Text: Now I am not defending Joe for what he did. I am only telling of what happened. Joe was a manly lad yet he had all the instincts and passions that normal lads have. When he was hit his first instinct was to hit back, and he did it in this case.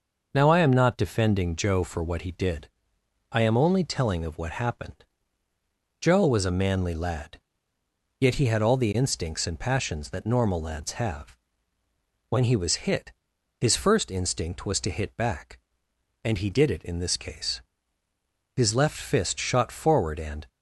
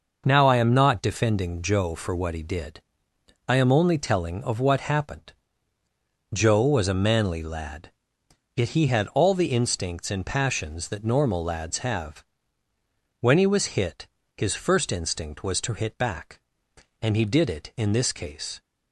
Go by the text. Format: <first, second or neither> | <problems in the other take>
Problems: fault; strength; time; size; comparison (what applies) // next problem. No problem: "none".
second | pauses between "lad" and "yet"; noticeable; at 7.3 s; 0.82 s long; noticeable in the second // pauses between "hit" and "his"; noticeable; at 13.1 s; 0.48 s long; slight in the second // goes on to say "His left fist shot forward and"; strong; from 18.5 s on; 1.9 s long